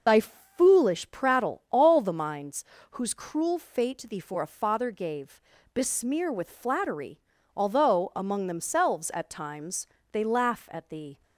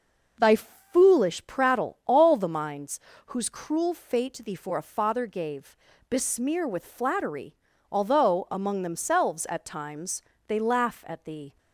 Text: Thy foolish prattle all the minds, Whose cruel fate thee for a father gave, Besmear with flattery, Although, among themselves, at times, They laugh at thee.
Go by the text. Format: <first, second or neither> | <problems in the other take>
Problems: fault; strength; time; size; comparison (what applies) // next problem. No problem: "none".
second | loses the start of "Thy"; at 0.0 s; 25 ms